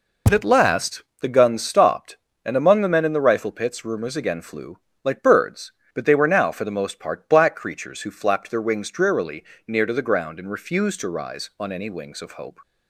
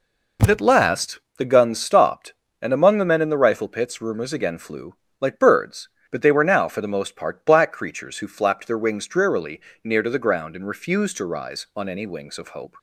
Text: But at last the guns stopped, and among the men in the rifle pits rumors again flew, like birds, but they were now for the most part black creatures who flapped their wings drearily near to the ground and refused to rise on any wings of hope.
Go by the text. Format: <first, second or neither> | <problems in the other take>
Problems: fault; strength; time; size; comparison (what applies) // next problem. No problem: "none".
second | loses the start of "But"; at 0.2 s; 25 ms // pauses between "last" and "the"; slight; at 1.0 s; 0.18 s long; slight in the second // pauses between "drearily" and "near"; slight; at 9.4 s; 0.22 s long; slight in the second